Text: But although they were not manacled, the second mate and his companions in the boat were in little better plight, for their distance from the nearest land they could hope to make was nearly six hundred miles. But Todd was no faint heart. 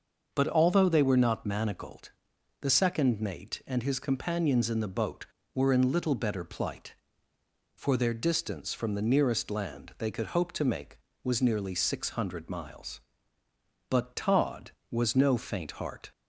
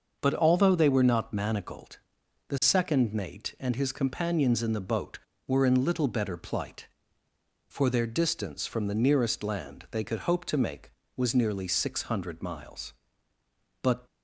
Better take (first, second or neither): first